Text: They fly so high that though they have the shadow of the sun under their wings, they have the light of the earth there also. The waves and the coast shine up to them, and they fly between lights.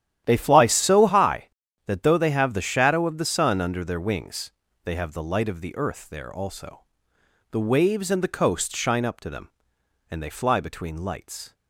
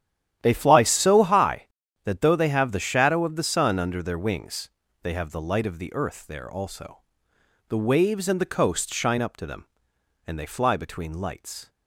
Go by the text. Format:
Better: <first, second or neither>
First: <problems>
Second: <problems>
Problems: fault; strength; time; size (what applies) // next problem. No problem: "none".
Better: neither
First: starts louder than the rest; strong; until 1.2 s; 11.5 dB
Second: starts louder than the rest; strong; until 1.4 s; 11.5 dB